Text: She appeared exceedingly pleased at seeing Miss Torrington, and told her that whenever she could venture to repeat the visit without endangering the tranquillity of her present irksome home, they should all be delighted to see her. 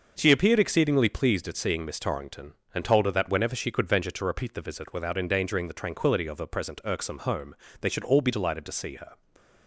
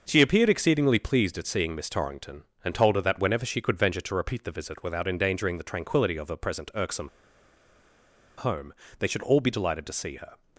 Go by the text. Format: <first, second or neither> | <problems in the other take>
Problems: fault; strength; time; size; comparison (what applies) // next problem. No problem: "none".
first | starts louder than the rest; noticeable; until 1.0 s; 6 dB; noticeable in the first // pauses between "irksome" and "home"; strong; at 7.0 s; 1.2 s long